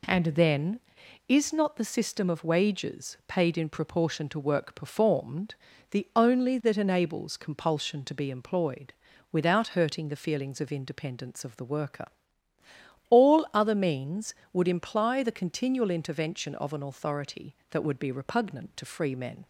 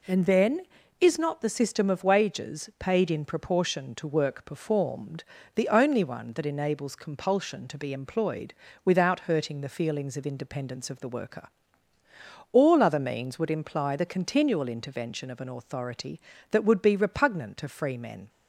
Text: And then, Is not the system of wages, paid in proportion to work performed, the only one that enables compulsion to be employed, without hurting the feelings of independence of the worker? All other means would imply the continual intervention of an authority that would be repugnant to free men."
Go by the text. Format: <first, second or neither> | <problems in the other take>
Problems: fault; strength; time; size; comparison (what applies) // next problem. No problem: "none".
second | skips "one"; at 6.6 s